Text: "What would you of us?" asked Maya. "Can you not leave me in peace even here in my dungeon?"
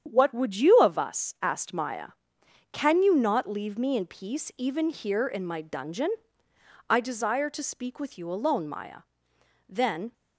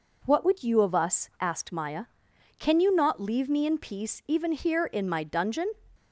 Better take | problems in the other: second | starts louder than the rest; strong; until 1.0 s; 8.5 dB // goes on to say "I desire to speak with you alone Maya Then"; strong; from 6.8 s on; 3.2 s long

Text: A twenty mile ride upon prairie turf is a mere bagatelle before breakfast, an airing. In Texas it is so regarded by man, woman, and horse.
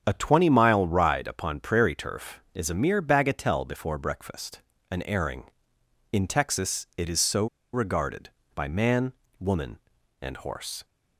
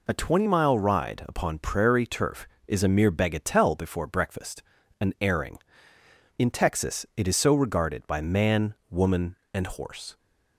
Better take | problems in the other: second | starts louder than the rest; strong; until 1.0 s; 8 dB // pauses between "so" and "regarded"; slight; at 7.4 s; 0.27 s long

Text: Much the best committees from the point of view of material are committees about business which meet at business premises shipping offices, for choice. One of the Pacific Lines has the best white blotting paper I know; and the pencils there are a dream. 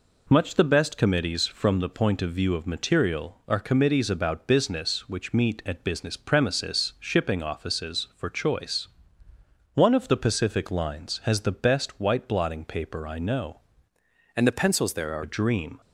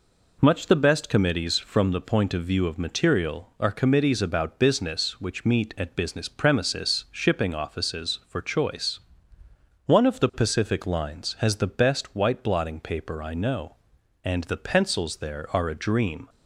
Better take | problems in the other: second | changes voice from "and" to "are"; from 14.3 to 15.2 s; 0.9 s long

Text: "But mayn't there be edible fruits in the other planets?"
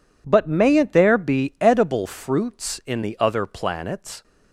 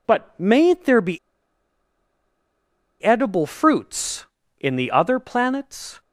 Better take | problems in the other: first | pauses between "be" and "edible"; strong; at 1.1 s; 1.8 s long

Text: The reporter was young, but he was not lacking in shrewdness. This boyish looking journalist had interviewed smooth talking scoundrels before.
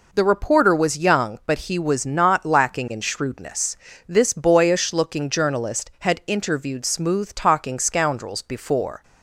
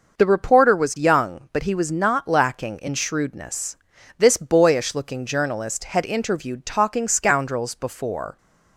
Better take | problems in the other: first | starts louder than the rest; noticeable; until 1.2 s; 6 dB // skips "smooth"; at 6.6 s

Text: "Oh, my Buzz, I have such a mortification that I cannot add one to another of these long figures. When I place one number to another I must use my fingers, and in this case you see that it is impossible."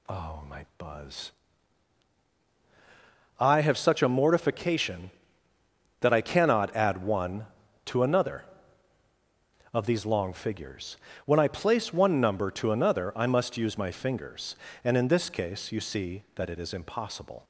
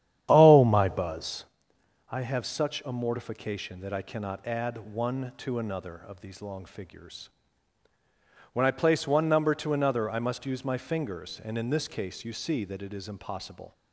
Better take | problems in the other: first | starts louder than the rest; strong; until 1.4 s; 10 dB

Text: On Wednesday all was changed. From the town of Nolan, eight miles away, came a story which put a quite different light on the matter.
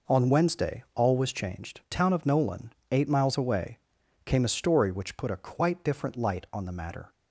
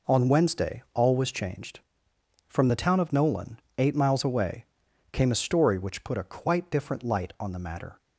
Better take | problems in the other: second | skips "From the"; at 1.8 s

